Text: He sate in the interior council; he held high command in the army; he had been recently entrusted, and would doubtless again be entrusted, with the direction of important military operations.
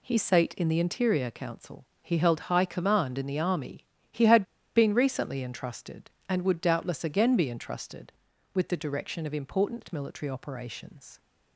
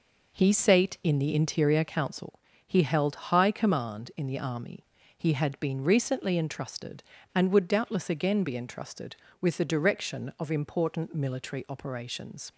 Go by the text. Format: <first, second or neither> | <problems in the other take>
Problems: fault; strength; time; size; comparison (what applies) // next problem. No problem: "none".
second | pauses between "had" and "been"; slight; at 4.4 s; 0.33 s long